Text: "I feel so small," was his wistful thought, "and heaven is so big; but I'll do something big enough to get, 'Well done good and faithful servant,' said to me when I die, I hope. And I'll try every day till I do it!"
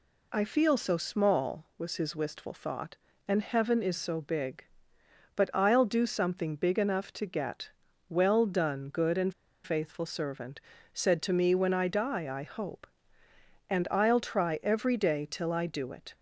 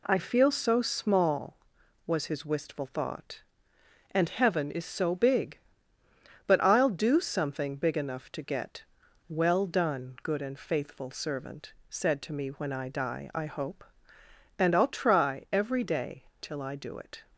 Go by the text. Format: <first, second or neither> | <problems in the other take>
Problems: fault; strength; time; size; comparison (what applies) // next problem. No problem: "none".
second | pauses between "and" and "faithful"; slight; at 9.3 s; 0.31 s long